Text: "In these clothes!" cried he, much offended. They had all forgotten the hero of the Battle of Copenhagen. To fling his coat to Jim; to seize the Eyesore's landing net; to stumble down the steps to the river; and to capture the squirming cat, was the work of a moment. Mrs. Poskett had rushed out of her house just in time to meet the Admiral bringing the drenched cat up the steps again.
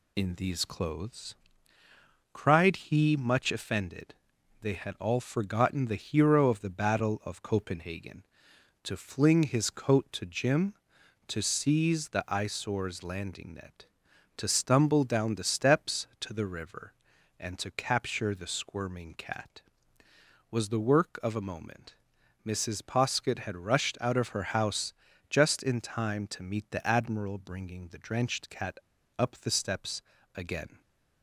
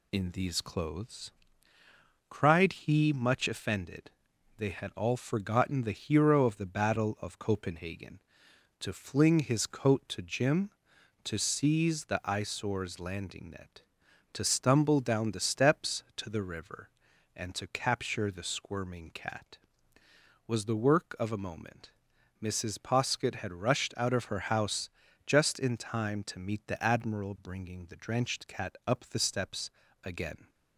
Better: second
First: pauses between "house" and "just"; slight; at 24.9 s; 0.36 s long // pauses between "cat" and "up"; at 28.7 s; 0.41 s long // pauses between "steps" and "again"; slight; at 30.0 s; 0.36 s long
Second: pauses between "house" and "just"; slight; at 24.8 s; 0.36 s long // pauses between "steps" and "again"; slight; at 29.6 s; 0.36 s long

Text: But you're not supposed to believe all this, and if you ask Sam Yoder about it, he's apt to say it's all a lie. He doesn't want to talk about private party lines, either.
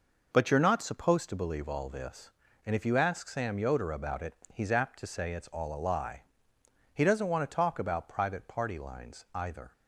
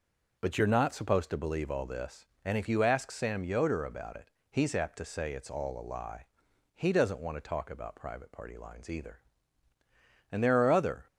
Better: first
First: none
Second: goes on to say "And there are other"; noticeable; from 10.3 s on; 0.76 s long

